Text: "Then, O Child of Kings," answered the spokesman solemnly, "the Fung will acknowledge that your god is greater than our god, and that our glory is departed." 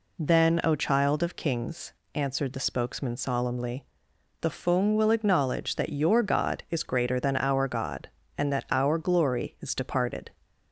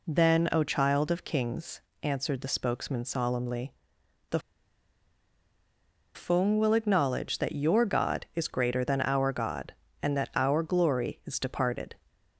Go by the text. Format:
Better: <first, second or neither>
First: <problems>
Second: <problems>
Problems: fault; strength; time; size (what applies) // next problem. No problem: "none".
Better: first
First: none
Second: pauses between "the" and "Fung"; strong; at 4.3 s; 1.7 s long